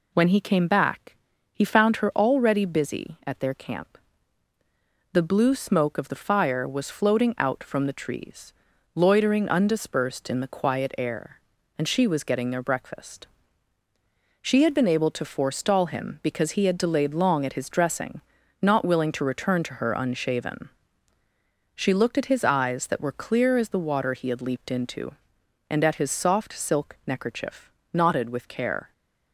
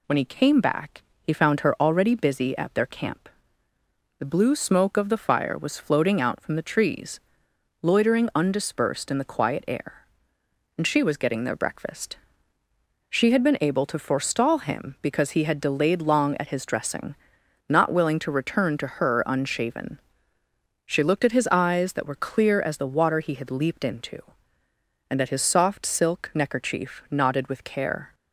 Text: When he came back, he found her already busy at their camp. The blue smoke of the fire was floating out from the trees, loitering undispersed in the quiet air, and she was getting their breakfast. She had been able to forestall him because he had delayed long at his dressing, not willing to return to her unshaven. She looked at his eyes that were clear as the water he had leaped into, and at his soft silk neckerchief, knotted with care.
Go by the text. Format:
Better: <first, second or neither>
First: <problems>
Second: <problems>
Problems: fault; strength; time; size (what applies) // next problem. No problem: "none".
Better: neither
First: none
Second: none